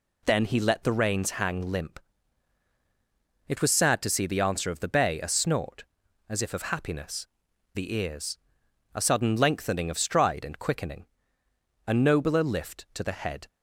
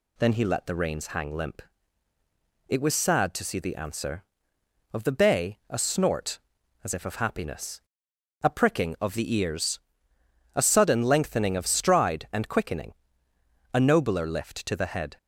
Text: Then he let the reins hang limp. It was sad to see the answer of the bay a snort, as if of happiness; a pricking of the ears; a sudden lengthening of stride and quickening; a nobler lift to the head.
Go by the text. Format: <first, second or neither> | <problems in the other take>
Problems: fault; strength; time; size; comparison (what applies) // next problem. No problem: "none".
second | skips "a pricking of"; at 7.5 s